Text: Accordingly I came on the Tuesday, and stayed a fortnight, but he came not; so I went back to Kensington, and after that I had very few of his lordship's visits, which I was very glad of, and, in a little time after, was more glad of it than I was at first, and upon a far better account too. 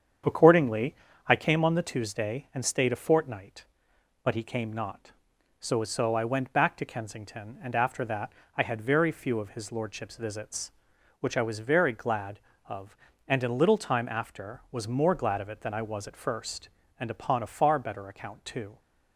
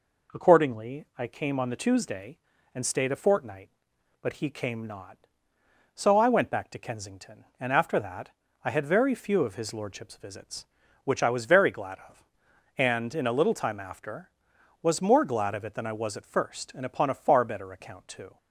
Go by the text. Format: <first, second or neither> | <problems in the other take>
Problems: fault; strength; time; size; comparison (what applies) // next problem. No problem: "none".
second | starts louder than the rest; strong; until 1.5 s; 8 dB // pauses between "Accordingly" and "I"; slight; at 0.9 s; 0.32 s long // says "so" twice; at 5.8 s // pauses between "that" and "I"; slight; at 8.3 s; 0.24 s long; slight in the second